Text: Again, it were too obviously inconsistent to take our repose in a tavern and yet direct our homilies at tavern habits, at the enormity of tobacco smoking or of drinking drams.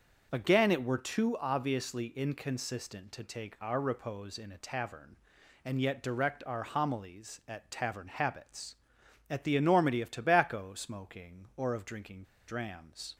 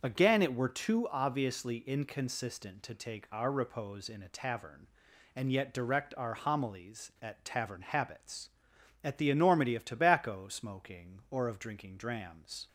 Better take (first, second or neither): second